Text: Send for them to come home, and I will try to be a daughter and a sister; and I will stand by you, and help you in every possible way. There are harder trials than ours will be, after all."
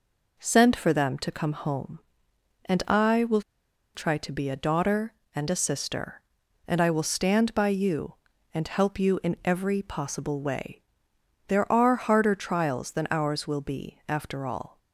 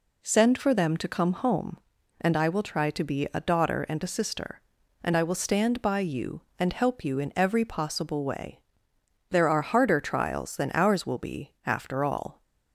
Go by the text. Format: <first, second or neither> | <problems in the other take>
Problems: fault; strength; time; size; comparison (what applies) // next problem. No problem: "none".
second | pauses between "will" and "try"; noticeable; at 3.4 s; 0.54 s long